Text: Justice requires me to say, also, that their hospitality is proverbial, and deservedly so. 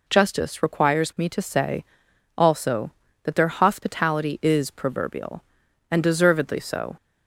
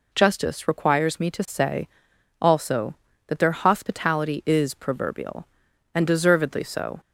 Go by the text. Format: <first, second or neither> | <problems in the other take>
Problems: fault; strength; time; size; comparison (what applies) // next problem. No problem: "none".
neither | none